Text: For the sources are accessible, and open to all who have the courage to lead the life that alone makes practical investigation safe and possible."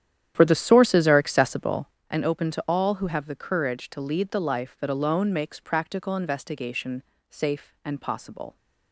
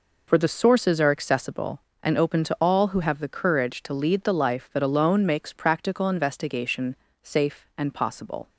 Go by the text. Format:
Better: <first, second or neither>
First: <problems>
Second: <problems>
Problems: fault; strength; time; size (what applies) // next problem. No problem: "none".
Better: second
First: starts louder than the rest; strong; until 2.1 s; 10.5 dB // pauses between "investigation" and "safe"; slight; at 7.0 s; 0.28 s long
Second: pauses between "investigation" and "safe"; slight; at 6.9 s; 0.28 s long